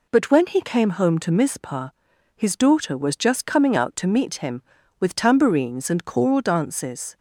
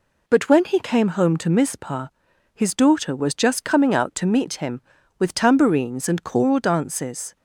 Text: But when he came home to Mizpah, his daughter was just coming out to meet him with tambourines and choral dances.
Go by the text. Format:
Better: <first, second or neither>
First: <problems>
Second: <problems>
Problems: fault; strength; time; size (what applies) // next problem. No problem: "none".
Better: neither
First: none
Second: none